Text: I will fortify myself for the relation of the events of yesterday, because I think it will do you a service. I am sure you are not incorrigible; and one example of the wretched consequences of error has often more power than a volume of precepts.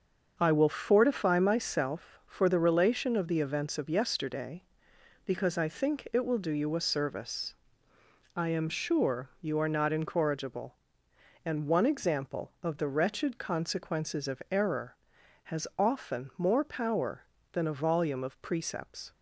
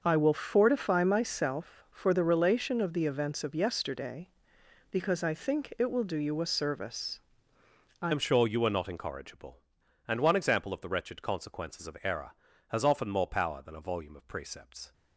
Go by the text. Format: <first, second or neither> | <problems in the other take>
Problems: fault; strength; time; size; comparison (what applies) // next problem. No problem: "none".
first | starts louder than the rest; until 1.0 s; 6.5 dB; also in the first // changes voice at "am"; from 8.1 s on; 6.8 s long